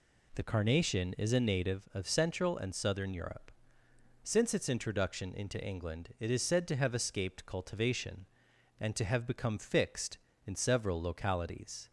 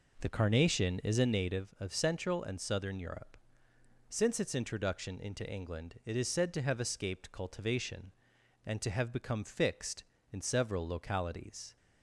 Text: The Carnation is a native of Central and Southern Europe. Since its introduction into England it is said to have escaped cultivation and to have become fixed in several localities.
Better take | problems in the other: first | starts louder than the rest; noticeable; until 1.5 s; 5 dB

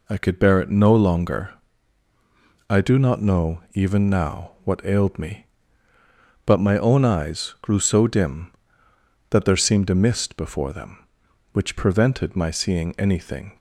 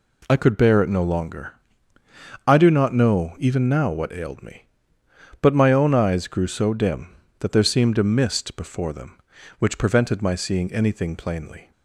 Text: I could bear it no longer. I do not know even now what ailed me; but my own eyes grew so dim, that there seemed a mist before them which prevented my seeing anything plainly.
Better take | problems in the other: second | stops before "plainly"; at 13.5 s

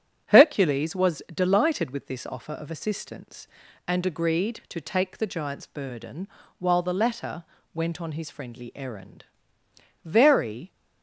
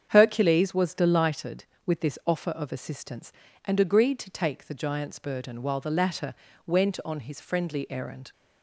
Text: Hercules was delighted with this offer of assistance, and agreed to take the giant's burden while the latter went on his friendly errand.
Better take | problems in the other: second | starts louder than the rest; strong; until 1.3 s; 7.5 dB; strong in the second // pauses between "burden" and "while"; slight; at 6.2 s; 0.32 s long // pauses between "latter" and "went"; slight; at 7.4 s; 0.30 s long; slight in the second // goes on to say "Very"; noticeable; from 10.0 s on; 0.68 s long

